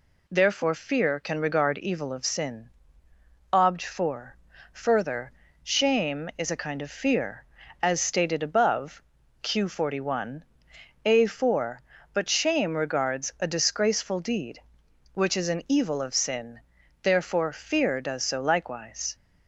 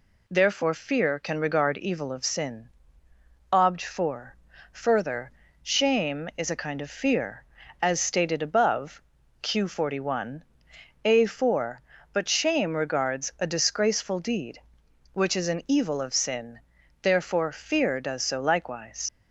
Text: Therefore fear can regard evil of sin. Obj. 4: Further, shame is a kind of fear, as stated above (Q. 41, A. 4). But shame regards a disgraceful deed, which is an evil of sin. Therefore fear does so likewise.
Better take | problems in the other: first | leaves "likewise" unfinished; at 19.0 s; 55 ms

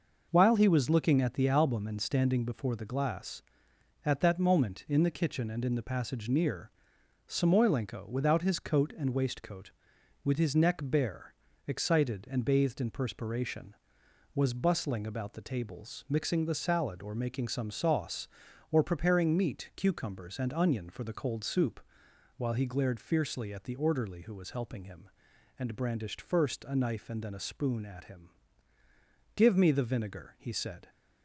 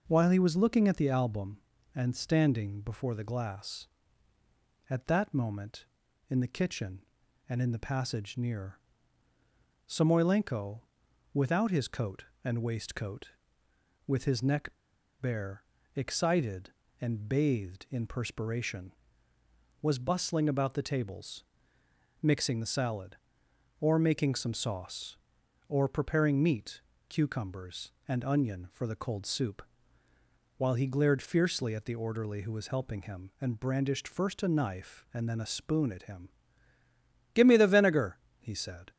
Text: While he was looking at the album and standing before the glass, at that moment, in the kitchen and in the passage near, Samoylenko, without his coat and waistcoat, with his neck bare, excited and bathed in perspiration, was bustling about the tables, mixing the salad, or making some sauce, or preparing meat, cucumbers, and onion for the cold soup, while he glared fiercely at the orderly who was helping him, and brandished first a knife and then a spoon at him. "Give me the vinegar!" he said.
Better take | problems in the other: first | pauses between "neck" and "bare"; noticeable; at 14.6 s; 0.52 s long

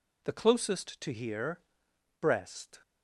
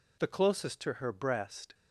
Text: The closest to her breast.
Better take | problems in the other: second | says "here" for "her"; at 1.1 s

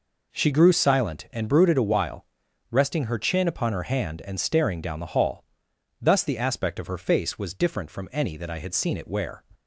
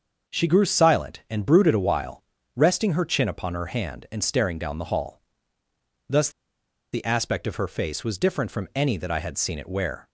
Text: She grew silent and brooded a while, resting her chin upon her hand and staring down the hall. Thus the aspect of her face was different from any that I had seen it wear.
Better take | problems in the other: first | starts louder than the rest; until 1.3 s; 6 dB // pauses between "Thus" and "the"; noticeable; at 6.2 s; 0.63 s long

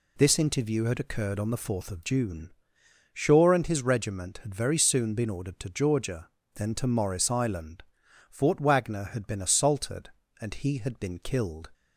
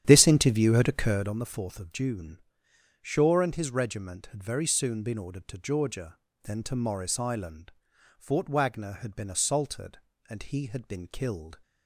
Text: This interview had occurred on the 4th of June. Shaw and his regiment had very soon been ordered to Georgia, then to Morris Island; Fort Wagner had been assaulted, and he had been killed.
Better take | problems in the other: first | starts louder than the rest; strong; until 1.4 s; 10 dB

